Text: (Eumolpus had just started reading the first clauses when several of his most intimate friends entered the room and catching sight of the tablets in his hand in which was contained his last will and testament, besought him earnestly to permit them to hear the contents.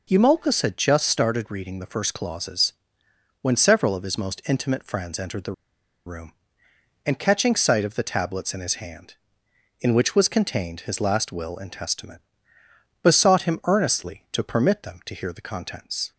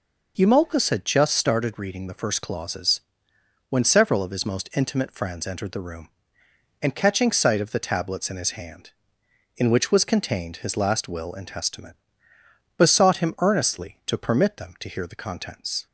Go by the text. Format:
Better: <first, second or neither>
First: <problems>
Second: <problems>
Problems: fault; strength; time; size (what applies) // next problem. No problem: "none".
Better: second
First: pauses between "clauses" and "when"; noticeable; at 2.7 s; 0.70 s long // pauses between "the" and "room"; noticeable; at 5.5 s; 0.53 s long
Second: pauses between "clauses" and "when"; noticeable; at 3.0 s; 0.70 s long